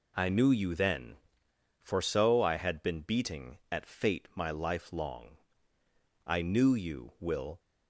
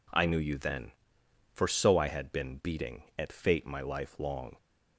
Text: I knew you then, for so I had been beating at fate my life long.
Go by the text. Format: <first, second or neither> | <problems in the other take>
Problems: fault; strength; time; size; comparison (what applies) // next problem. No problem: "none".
second | goes on to say "I knew you Will"; from 6.2 s on; 1.3 s long